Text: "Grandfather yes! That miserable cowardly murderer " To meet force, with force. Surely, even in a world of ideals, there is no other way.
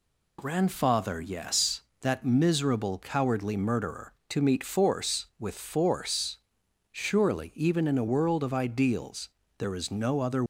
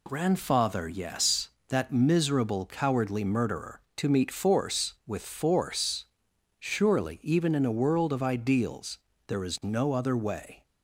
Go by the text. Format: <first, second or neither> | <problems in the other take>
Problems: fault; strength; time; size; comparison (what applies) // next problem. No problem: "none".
second | stops before "way"; at 10.4 s